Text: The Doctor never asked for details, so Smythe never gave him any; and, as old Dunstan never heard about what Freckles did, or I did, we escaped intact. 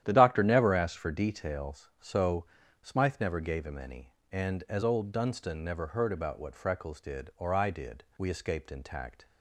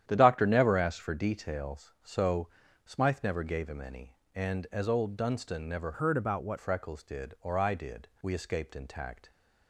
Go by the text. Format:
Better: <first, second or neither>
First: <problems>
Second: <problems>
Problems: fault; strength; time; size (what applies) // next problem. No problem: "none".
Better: first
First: starts louder than the rest; strong; until 1.0 s; 11 dB // pauses between "so" and "Smythe"; at 2.4 s; 0.38 s long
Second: starts louder than the rest; strong; until 1.0 s; 10.5 dB // pauses between "so" and "Smythe"; at 2.4 s; 0.38 s long // changes voice from "heard" to "what"; from 5.9 to 6.5 s; 0.6 s long